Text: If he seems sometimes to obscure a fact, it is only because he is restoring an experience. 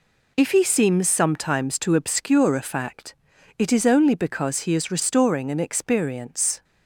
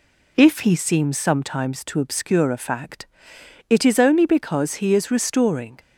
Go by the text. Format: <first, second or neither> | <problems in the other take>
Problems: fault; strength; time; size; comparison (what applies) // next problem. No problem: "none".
first | stops before "an experience"; at 5.7 s